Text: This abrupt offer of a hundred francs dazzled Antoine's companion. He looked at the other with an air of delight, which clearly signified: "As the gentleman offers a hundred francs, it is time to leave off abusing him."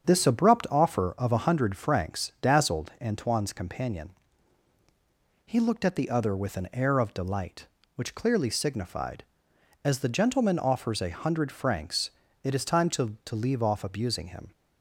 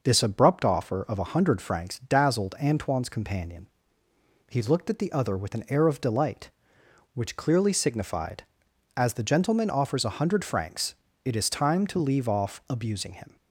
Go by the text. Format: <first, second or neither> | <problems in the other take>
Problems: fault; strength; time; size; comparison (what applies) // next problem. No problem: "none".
second | starts louder than the rest; strong; until 1.0 s; 7.5 dB // says "to" twice; at 13.2 s